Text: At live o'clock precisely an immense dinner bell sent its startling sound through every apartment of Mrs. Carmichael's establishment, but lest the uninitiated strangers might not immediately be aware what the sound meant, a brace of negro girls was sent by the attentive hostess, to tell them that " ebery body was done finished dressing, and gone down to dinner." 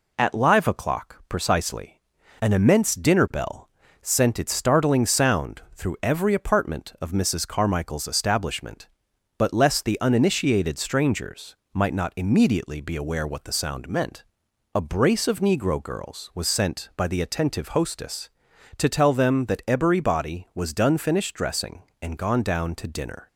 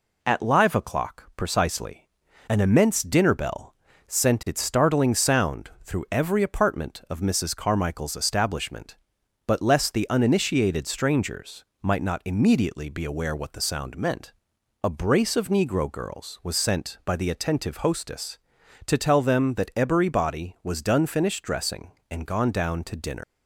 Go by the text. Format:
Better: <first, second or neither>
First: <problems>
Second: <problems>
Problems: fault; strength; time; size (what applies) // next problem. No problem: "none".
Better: first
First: pauses between "precisely" and "an"; at 1.9 s; 0.40 s long // pauses between "bell" and "sent"; slight; at 3.6 s; 0.34 s long // pauses between "strangers" and "might"; slight; at 11.5 s; 0.18 s long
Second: pauses between "precisely" and "an"; at 2.0 s; 0.40 s long // pauses between "bell" and "sent"; slight; at 3.7 s; 0.34 s long // pauses between "strangers" and "might"; slight; at 11.6 s; 0.18 s long // leaves "dinner" unfinished; at 23.2 s; 125 ms